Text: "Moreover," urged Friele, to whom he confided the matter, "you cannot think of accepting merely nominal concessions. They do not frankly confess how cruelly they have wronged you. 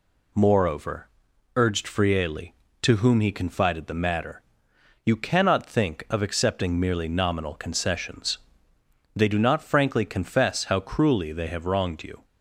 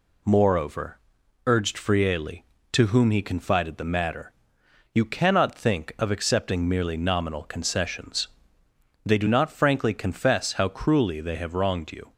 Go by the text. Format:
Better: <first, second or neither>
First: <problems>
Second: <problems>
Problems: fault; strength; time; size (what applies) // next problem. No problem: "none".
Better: neither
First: none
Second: none